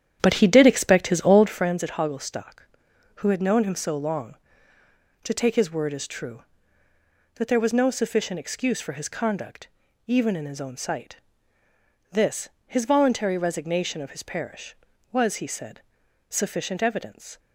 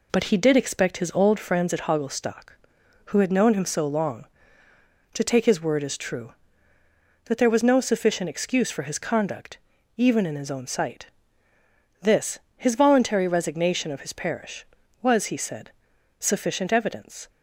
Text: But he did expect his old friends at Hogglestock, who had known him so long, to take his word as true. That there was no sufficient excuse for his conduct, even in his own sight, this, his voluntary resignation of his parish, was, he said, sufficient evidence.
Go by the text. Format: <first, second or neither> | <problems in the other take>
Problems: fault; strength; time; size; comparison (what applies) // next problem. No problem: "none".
second | starts louder than the rest; strong; until 1.7 s; 9.5 dB